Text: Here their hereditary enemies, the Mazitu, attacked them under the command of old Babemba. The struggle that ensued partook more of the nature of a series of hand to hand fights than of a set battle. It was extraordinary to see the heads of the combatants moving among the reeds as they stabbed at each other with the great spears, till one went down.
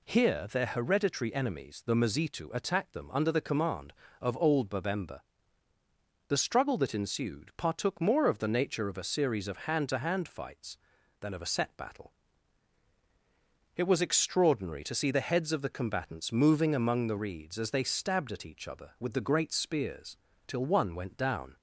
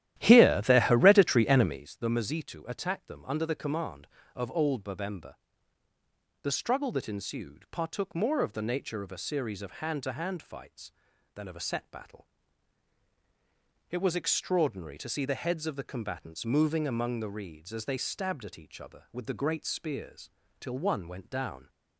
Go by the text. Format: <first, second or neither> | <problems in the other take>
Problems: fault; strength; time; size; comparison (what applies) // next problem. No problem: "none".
first | starts louder than the rest; strong; until 2.0 s; 12.5 dB